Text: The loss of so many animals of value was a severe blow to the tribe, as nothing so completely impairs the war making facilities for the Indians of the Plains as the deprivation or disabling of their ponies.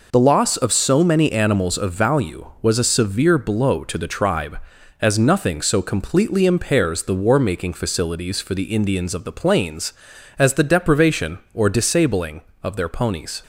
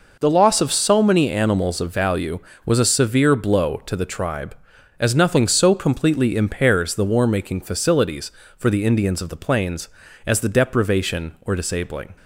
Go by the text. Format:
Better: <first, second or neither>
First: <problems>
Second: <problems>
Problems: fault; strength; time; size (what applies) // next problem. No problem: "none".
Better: first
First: none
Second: stops before "of their ponies"; at 12.1 s